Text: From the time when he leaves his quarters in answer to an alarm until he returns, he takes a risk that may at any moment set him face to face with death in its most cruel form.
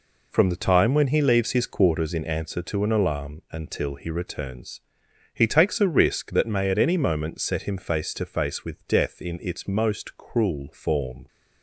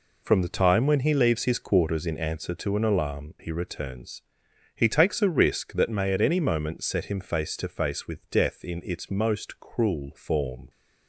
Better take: first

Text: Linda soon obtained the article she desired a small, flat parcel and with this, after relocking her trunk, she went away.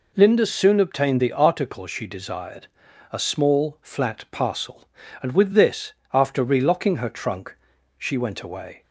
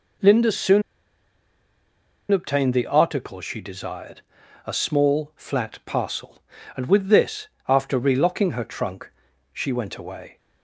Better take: first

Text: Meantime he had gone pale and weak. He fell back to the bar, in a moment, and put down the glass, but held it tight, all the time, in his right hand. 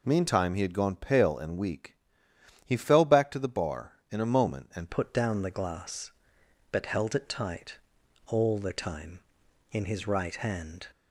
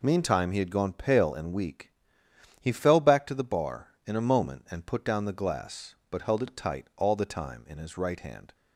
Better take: second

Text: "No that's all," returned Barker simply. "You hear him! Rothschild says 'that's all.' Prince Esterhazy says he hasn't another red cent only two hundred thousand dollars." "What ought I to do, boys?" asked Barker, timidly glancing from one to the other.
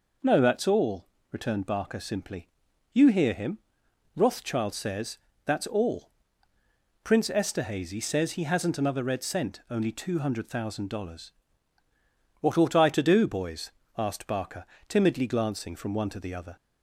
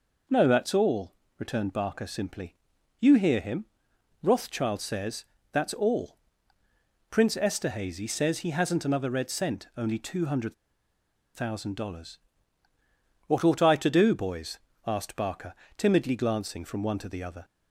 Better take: first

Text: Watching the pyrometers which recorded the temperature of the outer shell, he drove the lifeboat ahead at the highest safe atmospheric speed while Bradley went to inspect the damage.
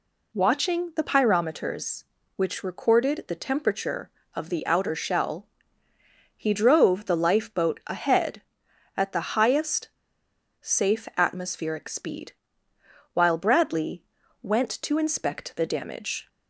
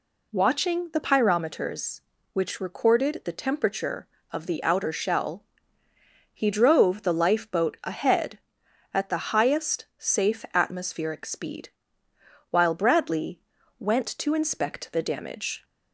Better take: second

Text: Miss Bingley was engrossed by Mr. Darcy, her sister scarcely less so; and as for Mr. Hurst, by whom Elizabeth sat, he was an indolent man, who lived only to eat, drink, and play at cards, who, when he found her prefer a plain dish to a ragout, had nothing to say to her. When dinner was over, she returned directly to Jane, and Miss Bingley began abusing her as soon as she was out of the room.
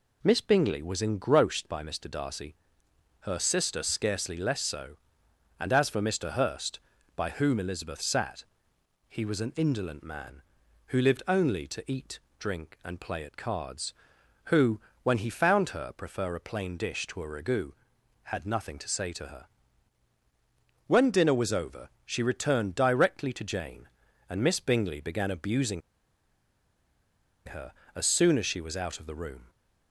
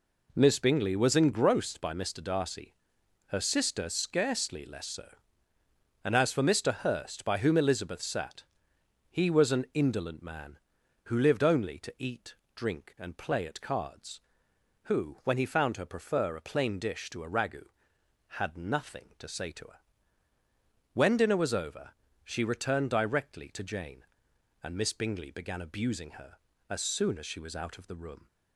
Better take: second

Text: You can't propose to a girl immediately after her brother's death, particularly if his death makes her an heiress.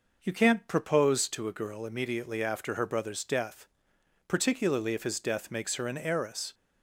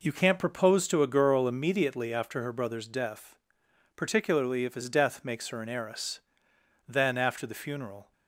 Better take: first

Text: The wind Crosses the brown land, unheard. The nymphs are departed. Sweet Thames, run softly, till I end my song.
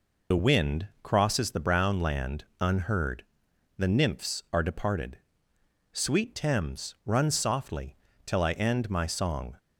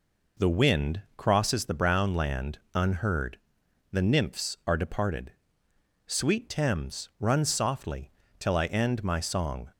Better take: second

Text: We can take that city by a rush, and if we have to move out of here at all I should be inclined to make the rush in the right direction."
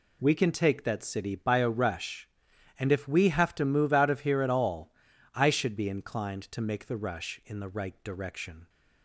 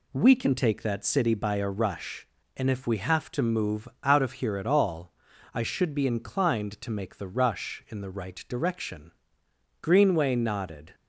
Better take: first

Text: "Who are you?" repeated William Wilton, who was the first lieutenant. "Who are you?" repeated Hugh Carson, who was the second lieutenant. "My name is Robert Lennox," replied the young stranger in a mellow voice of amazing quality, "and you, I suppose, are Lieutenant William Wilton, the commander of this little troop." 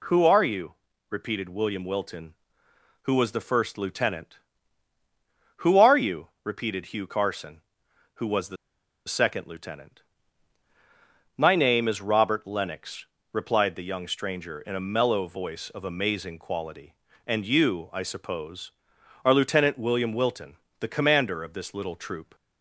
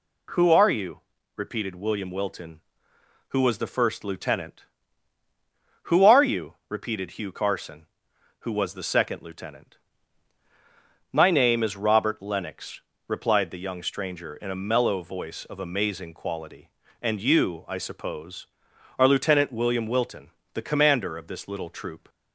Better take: second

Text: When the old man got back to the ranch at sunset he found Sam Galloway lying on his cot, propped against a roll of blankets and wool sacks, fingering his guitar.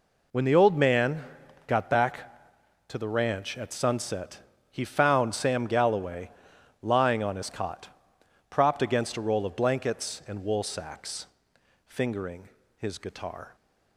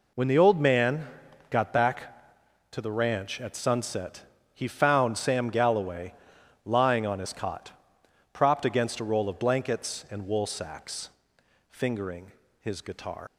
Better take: first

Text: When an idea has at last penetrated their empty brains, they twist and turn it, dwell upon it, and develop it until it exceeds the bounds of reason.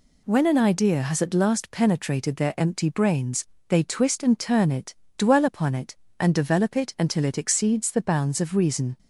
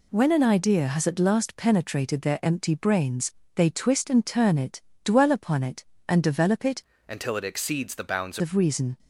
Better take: first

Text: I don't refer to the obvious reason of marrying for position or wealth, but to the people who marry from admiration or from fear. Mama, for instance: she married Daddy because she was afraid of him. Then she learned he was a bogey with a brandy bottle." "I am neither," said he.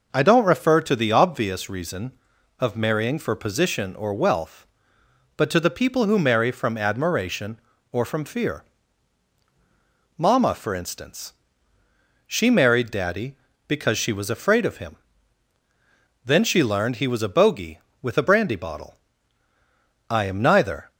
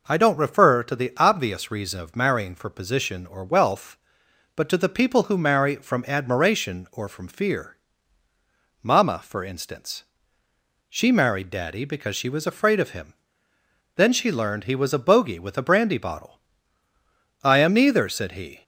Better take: second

